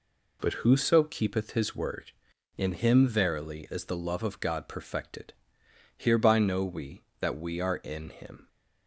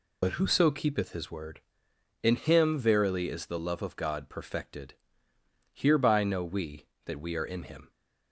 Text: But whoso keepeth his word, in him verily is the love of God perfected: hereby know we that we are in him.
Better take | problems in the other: first | loses the start of "But"; at 0.2 s; 55 ms

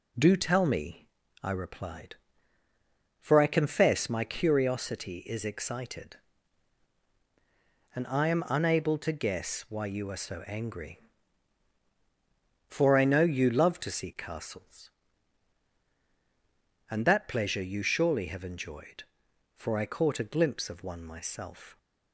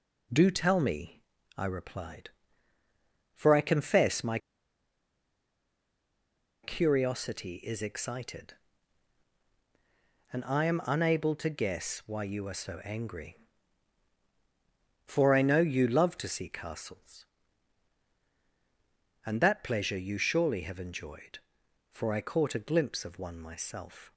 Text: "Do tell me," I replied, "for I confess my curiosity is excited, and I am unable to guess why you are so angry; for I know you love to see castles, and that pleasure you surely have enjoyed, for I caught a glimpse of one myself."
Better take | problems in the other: first | pauses between "my" and "curiosity"; strong; at 4.3 s; 2.2 s long

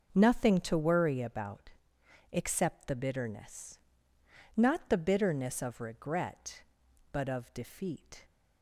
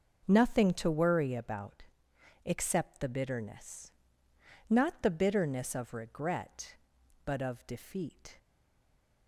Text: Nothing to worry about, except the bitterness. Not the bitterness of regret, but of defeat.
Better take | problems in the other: first | starts louder than the rest; noticeable; until 1.2 s; 6 dB; noticeable in the first // stays silent after the last word; slight; from 8.3 s on; 0.9 s long

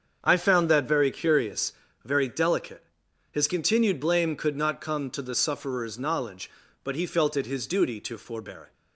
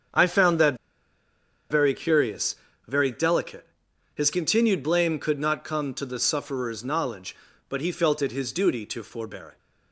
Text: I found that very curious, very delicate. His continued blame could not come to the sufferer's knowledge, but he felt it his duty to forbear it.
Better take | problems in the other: first | starts louder than the rest; until 2.0 s; 7 dB; also in the first // pauses between "that" and "very"; noticeable; at 0.7 s; 0.95 s long

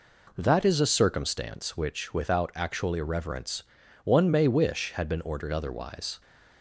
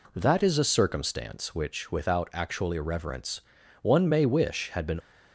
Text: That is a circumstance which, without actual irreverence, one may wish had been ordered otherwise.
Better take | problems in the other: first | stops before "ordered otherwise"; at 5.0 s

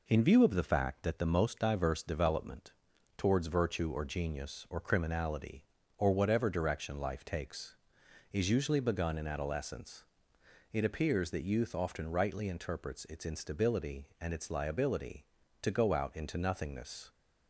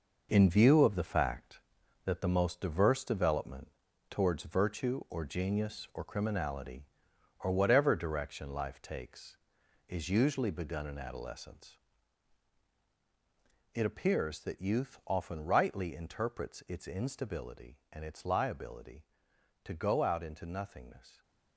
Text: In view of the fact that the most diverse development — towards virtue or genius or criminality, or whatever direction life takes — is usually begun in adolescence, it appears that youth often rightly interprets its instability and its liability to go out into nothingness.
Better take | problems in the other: first | gets quieter; strong; throughout; 8.5 dB

